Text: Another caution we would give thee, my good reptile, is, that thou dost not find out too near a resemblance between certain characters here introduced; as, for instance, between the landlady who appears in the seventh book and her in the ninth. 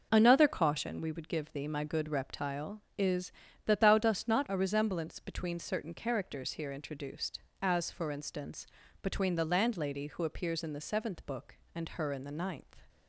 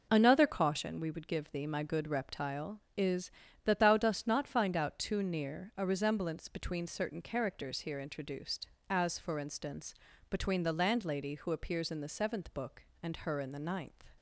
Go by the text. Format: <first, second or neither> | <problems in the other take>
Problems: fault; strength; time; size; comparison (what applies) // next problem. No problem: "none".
second | skips "find out too near"; at 4.4 s